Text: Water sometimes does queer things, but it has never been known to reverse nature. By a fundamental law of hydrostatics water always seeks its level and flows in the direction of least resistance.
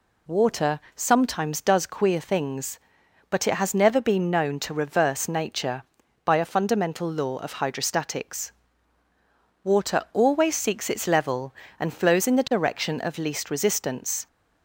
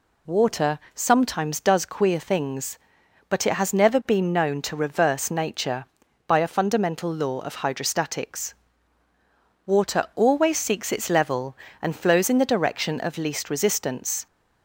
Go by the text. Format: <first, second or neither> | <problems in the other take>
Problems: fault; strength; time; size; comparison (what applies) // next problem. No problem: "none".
neither | pauses between "Water" and "sometimes"; slight; the same in both // pauses between "hydrostatics" and "water"; the same in both